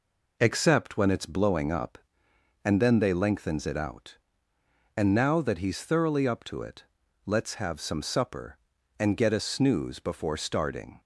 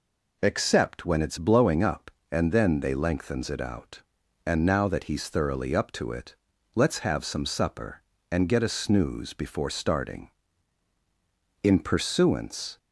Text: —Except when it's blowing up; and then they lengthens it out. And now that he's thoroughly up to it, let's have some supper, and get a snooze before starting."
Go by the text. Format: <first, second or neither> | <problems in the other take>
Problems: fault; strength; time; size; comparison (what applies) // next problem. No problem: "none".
first | goes on to say "In pursuance"; noticeable; from 11.6 s on; 1.1 s long